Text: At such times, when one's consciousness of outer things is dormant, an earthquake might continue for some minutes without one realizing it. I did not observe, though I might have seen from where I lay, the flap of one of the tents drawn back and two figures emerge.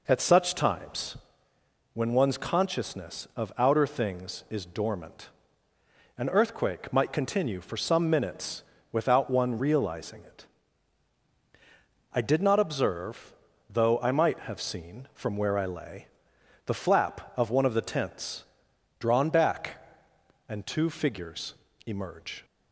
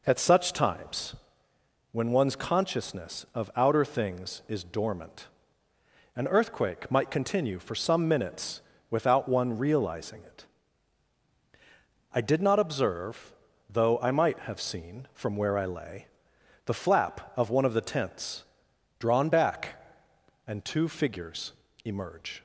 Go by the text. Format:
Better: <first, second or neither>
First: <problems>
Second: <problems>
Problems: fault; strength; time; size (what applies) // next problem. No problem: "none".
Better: neither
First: pauses between "minutes" and "without"; slight; at 8.6 s; 0.30 s long // pauses between "tents" and "drawn"; noticeable; at 18.4 s; 0.54 s long // pauses between "figures" and "emerge"; slight; at 21.5 s; 0.32 s long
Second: pauses between "minutes" and "without"; slight; at 8.6 s; 0.30 s long // pauses between "tents" and "drawn"; noticeable; at 18.4 s; 0.54 s long // pauses between "figures" and "emerge"; slight; at 21.5 s; 0.32 s long